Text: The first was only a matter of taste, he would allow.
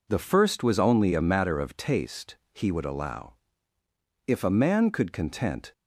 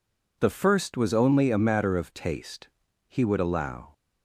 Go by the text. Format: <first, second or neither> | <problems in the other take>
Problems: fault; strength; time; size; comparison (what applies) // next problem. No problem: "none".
second | goes on to say "If a man could content"; from 4.2 s on; 1.4 s long